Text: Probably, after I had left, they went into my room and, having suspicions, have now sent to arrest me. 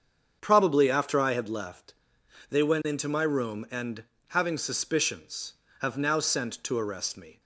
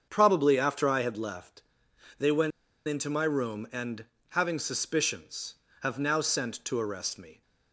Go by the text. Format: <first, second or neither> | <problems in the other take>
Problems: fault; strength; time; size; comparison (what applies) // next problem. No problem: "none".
first | starts louder than the rest; until 1.1 s; 7 dB; also in the first // pauses between "went" and "into"; at 2.5 s; 0.36 s long